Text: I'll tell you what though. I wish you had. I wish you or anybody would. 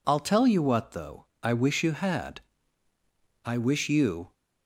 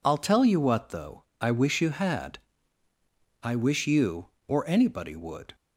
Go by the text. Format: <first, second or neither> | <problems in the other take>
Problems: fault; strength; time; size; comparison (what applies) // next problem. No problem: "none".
second | stops before "or anybody would"; at 4.3 s